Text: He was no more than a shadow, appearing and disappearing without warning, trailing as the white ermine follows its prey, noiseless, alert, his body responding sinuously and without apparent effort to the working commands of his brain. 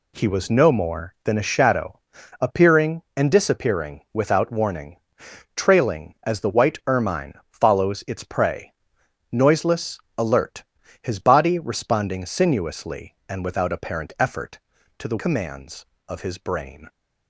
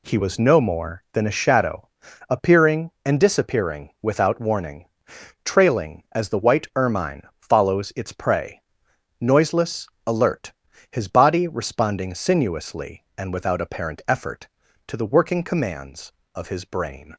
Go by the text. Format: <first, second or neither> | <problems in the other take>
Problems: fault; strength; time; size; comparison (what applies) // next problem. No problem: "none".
second | pauses between "ermine" and "follows"; slight; at 7.3 s; 0.18 s long; slight in the second // skips "working"; at 15.1 s